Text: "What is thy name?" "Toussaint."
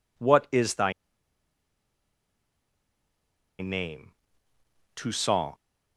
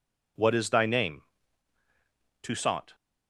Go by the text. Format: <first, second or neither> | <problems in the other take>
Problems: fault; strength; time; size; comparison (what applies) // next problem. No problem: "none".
second | pauses between "thy" and "name"; strong; at 0.9 s; 2.6 s long